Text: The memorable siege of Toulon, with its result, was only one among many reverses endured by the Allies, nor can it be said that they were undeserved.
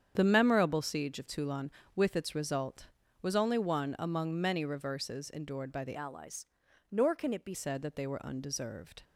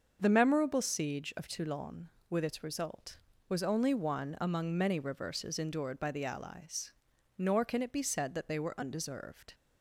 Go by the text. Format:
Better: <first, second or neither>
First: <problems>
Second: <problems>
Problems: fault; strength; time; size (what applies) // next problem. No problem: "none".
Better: second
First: starts louder than the rest; strong; until 1.1 s; 8 dB // changes voice from "Allies" to "be"; from 5.9 to 7.5 s; 1.6 s long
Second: starts louder than the rest; until 1.2 s; 6.5 dB